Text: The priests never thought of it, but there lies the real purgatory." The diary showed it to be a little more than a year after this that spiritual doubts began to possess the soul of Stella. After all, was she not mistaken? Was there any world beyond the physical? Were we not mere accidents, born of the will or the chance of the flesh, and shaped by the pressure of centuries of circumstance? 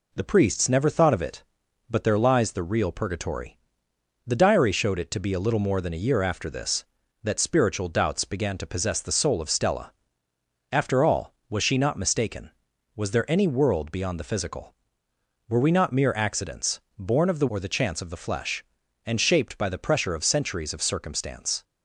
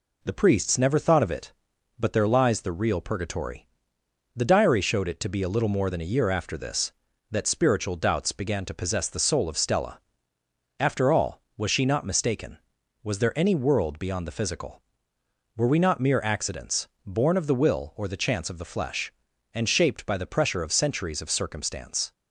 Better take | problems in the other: second | skips "will"; at 17.4 s

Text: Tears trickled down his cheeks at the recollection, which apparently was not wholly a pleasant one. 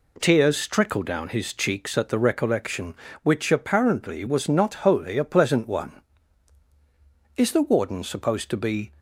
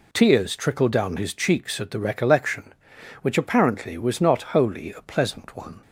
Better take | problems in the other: second | goes on to say "Is the Warden supposed to be"; from 7.3 s on; 1.5 s long

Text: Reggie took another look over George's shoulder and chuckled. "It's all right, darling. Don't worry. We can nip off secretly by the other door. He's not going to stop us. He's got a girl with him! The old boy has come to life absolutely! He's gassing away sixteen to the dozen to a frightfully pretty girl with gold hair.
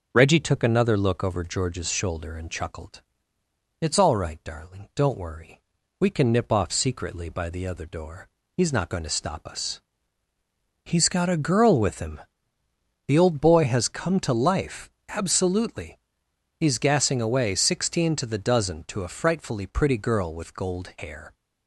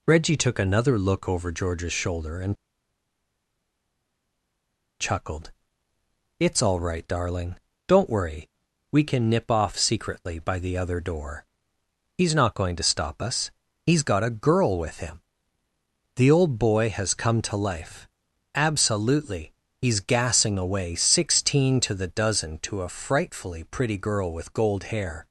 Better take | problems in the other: first | pauses between "and" and "chuckled"; strong; at 2.5 s; 2.4 s long // pauses between "life" and "absolutely"; noticeable; at 18.0 s; 0.48 s long; slight in the first

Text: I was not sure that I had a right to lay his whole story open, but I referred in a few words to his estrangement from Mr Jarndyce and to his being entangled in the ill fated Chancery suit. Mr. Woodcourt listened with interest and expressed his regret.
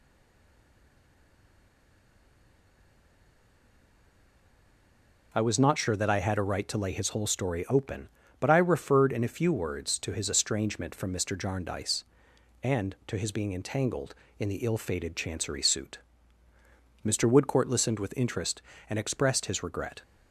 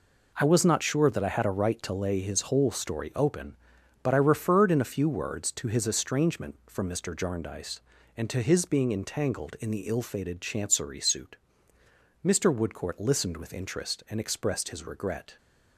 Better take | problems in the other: second | stays silent before the first word; strong; until 5.3 s; 5.3 s long

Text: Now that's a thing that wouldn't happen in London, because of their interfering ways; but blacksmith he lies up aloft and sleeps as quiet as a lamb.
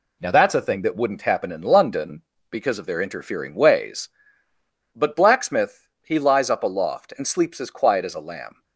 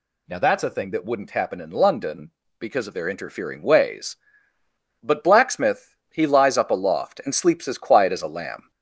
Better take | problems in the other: first | gets louder; slight; throughout; 2.5 dB // pauses between "blacksmith" and "he"; slight; at 5.9 s; 0.16 s long; slight in the first

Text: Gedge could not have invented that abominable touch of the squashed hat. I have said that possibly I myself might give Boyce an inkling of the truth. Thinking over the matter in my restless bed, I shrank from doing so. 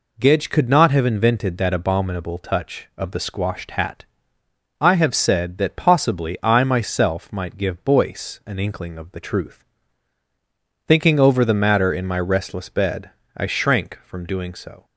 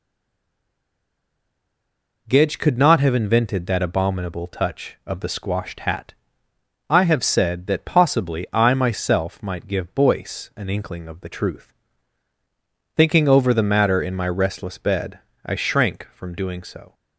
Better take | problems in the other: first | stays silent before the first word; until 2.2 s; 2.2 s long

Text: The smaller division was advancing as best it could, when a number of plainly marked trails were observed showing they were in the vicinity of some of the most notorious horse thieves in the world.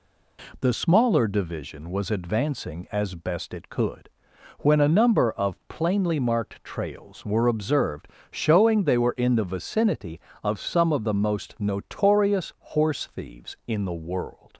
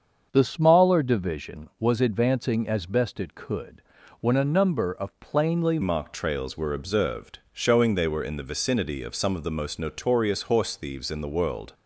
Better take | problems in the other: first | starts louder than the rest; until 1.3 s; 7 dB // changes voice at "marked"; from 5.8 s on; 5.9 s long // pauses between "observed" and "showing"; slight; at 7.3 s; 0.16 s long; slight in the first

